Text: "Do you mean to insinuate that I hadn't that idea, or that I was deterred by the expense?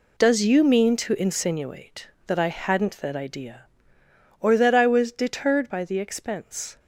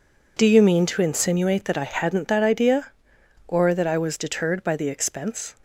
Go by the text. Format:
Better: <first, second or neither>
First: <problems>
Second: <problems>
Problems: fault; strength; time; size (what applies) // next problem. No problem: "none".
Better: second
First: says "Does" for "Do"; at 0.1 s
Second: none